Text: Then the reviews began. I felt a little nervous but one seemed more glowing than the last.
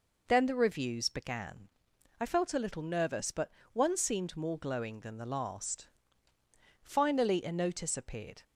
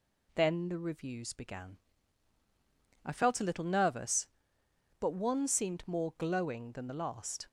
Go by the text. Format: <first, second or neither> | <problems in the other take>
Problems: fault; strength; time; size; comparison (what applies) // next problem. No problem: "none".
second | pauses between "but" and "one"; slight; at 3.5 s; 0.22 s long // goes on to say "Finally a notice appeared"; from 6.8 s on; 1.6 s long